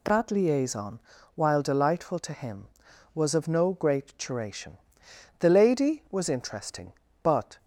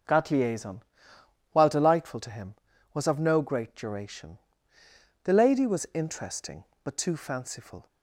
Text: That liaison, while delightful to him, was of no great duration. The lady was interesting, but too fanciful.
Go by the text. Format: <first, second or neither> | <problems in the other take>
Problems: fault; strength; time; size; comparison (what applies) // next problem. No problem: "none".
second | stops before "too fanciful"; at 7.5 s